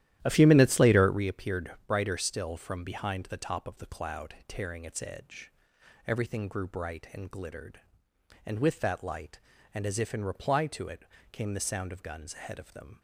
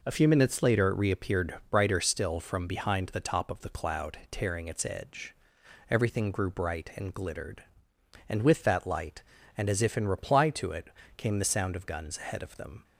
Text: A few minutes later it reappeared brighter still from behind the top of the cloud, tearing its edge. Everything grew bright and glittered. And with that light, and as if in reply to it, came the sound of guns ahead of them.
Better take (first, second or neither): second